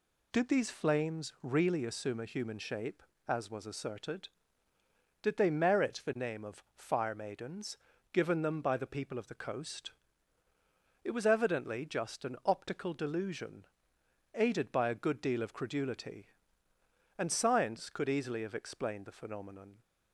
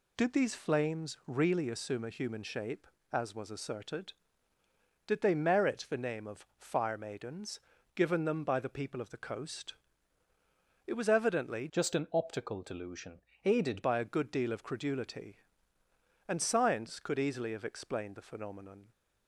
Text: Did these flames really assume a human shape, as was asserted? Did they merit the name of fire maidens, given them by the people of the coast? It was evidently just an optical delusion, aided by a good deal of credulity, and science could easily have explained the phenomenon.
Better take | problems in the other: first | changes voice from "just" to "aided"; from 11.6 to 13.8 s; 2.2 s long

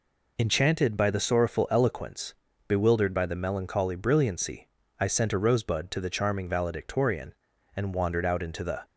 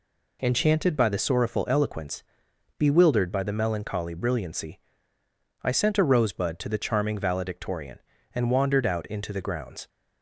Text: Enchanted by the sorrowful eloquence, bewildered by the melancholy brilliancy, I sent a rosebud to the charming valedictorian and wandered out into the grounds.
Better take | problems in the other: second | stops before "grounds"; at 8.8 s

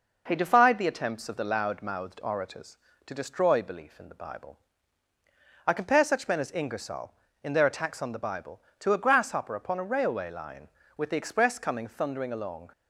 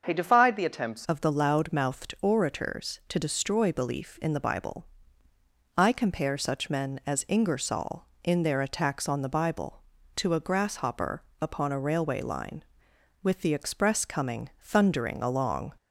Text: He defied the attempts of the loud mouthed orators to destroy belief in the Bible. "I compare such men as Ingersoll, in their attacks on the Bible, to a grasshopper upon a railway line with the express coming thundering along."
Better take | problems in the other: first | starts louder than the rest; until 1.0 s; 6.5 dB // changes voice at "of"; from 1.0 s on; 14.7 s long // pauses between "grasshopper" and "upon"; slight; at 11.2 s; 0.16 s long

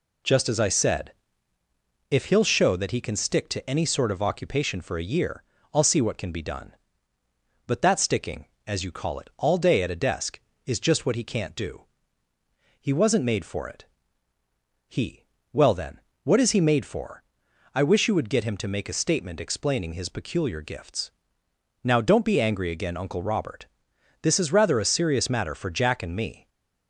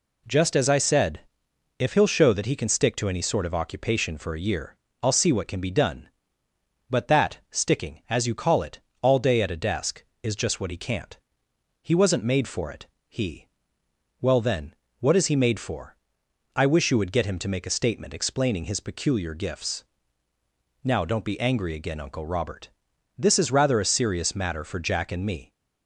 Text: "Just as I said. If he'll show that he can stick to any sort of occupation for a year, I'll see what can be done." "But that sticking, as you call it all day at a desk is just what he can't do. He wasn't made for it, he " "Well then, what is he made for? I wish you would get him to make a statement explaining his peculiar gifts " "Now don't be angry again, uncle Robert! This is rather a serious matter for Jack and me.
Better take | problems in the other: first | pauses between "it" and "all"; slight; at 8.7 s; 0.22 s long // skips "do"; at 11.5 s

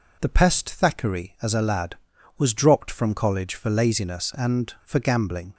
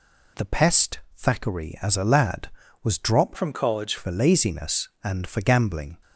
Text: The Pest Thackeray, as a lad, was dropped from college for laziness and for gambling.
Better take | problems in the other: first | pauses between "Pest" and "Thackeray"; slight; at 0.9 s; 0.18 s long // changes voice from "from" to "college"; from 3.3 to 3.9 s; 0.6 s long

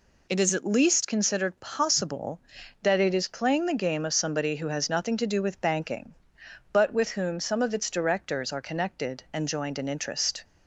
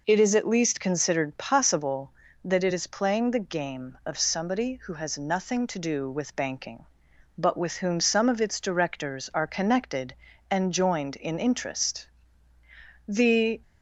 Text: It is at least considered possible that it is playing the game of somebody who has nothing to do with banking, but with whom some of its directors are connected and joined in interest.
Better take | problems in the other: first | goes on to say "The"; from 13.0 s on; 0.54 s long

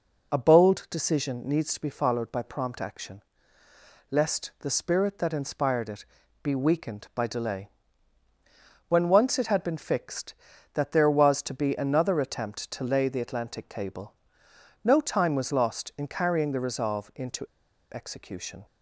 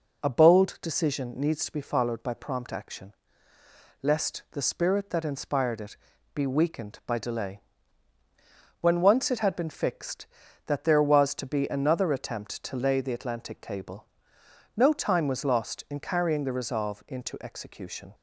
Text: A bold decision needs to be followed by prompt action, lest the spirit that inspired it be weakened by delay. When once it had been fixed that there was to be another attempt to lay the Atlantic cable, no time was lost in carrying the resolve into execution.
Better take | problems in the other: second | pauses between "it" and "be"; at 6.0 s; 0.38 s long; also in the second // pauses between "into" and "execution"; noticeable; at 17.4 s; 0.47 s long

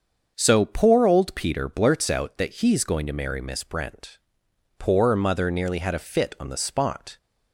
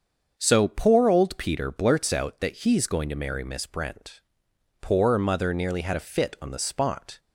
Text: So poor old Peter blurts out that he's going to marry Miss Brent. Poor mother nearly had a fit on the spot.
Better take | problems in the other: neither | starts louder than the rest; the same in both

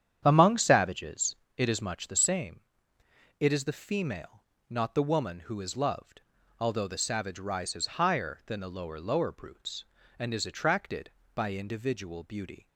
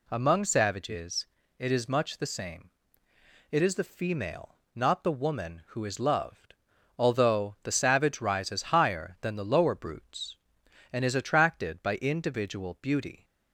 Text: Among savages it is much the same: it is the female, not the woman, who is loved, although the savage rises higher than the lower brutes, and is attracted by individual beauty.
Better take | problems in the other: second | starts louder than the rest; strong; until 1.2 s; 9 dB // pauses between "savages" and "it"; slight; at 1.3 s; 0.22 s long; slight in the second // says "lower" twice; at 9.0 s

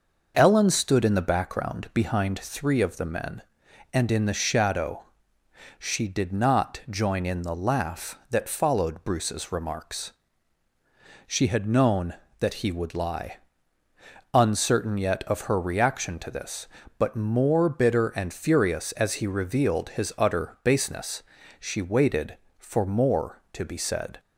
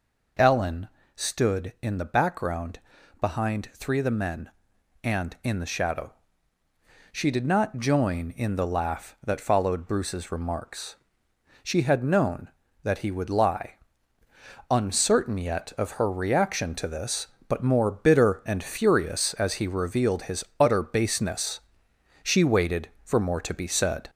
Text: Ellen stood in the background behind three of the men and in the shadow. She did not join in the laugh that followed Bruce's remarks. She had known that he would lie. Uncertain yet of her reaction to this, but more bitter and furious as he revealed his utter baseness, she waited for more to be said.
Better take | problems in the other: first | gets louder; throughout; 3.5 dB // pauses between "Ellen" and "stood"; slight; at 0.8 s; 0.28 s long // pauses between "background" and "behind"; at 2.7 s; 0.42 s long // pauses between "his" and "utter"; slight; at 20.4 s; 0.16 s long

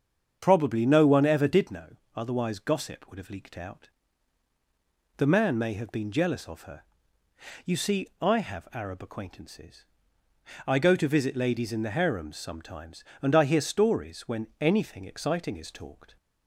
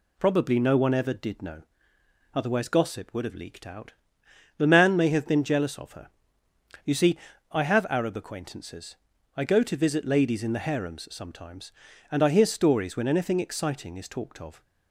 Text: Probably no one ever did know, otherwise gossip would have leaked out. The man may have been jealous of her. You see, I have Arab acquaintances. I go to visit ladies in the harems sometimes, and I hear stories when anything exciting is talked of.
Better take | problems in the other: second | starts louder than the rest; strong; until 1.4 s; 7 dB // stops before "of"; at 16.1 s

